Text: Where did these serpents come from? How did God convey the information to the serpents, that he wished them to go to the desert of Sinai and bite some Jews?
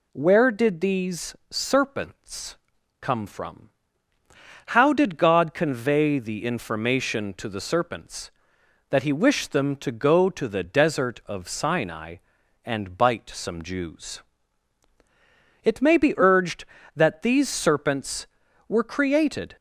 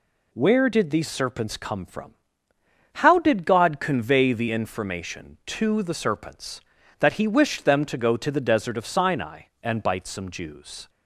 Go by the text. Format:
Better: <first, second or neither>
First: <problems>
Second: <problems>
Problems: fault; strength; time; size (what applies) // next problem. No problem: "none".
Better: second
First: pauses between "serpents" and "come"; at 2.5 s; 0.44 s long // goes on to say "It may be urged that these serpents were created"; strong; from 15.6 s on; 3.9 s long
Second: none